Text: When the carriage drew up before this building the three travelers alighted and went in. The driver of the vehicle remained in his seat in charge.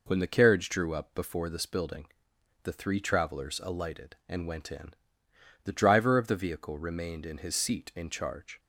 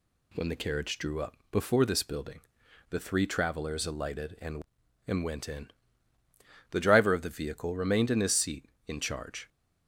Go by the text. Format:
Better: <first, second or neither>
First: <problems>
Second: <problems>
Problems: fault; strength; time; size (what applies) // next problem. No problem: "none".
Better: first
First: pauses between "building" and "the"; noticeable; at 2.0 s; 0.58 s long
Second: pauses between "building" and "the"; noticeable; at 2.4 s; 0.48 s long // says "and" twice; at 5.0 s